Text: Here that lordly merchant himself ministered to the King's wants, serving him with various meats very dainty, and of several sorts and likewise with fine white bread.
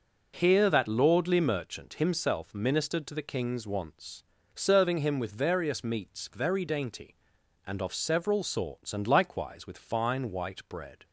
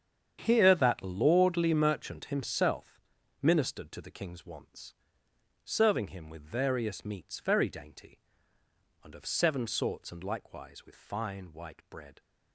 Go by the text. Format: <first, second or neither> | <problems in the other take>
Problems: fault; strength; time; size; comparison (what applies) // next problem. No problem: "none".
first | starts louder than the rest; strong; until 1.4 s; 8 dB // pauses between "himself" and "ministered"; at 3.0 s; 0.42 s long // says "seven" for "several"; at 9.2 s